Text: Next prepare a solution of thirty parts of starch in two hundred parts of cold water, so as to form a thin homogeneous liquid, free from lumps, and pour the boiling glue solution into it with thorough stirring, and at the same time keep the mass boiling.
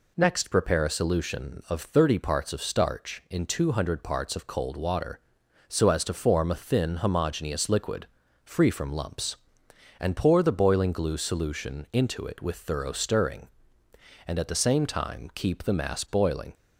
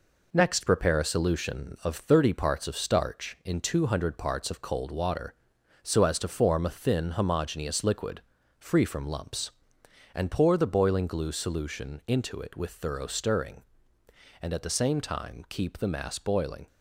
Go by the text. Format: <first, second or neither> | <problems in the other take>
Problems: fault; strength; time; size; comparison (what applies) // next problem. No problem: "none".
first | gets quieter; noticeable; throughout; 4.5 dB